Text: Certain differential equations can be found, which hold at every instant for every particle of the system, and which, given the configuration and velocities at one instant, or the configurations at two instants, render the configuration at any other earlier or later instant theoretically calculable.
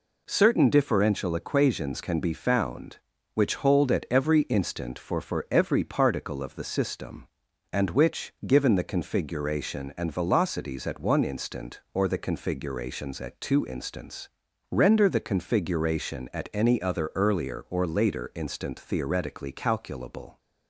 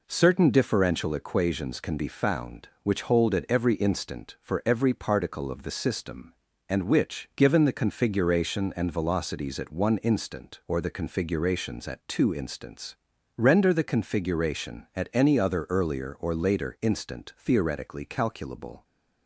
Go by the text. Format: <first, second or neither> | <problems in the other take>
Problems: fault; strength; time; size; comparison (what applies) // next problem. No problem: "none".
second | says "for" twice; at 5.1 s